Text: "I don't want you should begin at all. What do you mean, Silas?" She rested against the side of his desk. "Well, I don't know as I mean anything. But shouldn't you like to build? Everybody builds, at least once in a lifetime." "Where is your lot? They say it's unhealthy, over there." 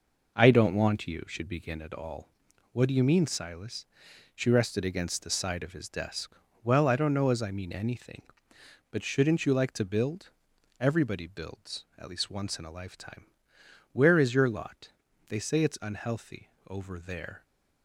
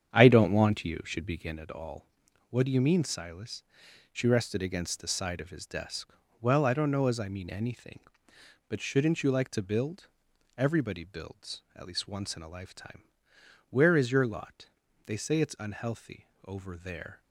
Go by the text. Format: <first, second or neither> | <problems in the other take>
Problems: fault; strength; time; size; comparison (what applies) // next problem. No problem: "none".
first | starts louder than the rest; strong; until 1.7 s; 8.5 dB